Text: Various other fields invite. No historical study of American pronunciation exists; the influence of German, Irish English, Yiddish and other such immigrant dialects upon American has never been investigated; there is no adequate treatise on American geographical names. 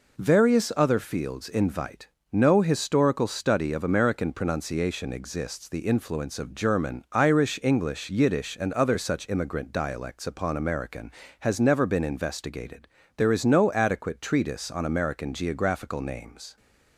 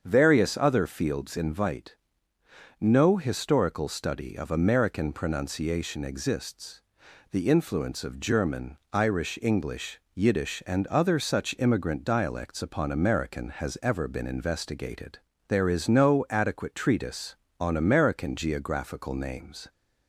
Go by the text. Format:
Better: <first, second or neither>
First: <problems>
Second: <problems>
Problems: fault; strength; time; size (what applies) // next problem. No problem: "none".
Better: first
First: none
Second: starts louder than the rest; until 1.0 s; 7 dB // says "ever" for "never"; at 13.8 s